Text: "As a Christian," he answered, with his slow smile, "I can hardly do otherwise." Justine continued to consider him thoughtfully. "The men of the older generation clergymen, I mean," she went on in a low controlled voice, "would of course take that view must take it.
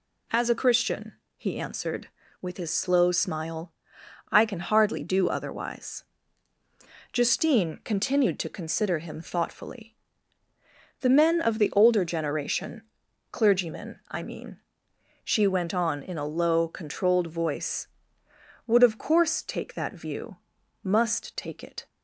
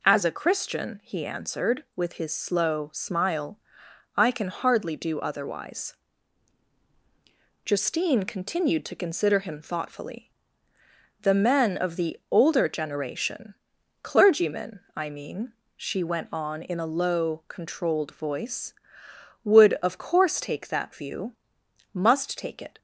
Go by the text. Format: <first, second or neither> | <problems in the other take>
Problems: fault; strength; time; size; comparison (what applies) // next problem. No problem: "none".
neither | pauses between "generation" and "clergymen"; noticeable; the same in both // pauses between "view" and "must"; noticeable; the same in both